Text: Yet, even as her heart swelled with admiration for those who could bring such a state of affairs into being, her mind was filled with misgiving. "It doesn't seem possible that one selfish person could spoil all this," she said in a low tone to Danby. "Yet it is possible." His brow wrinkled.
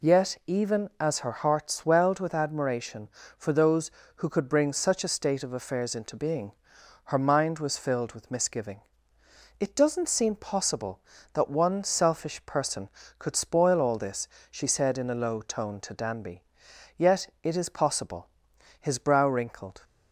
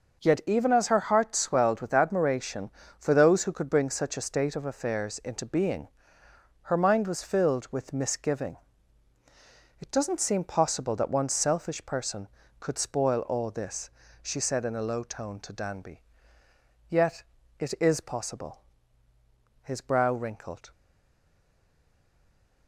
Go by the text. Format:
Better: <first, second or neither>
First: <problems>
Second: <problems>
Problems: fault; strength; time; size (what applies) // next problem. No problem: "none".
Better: first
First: none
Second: starts louder than the rest; until 1.2 s; 6.5 dB // pauses between "Yet" and "it"; slight; at 17.2 s; 0.34 s long // stays silent after the last word; noticeable; from 20.7 s on; 1.9 s long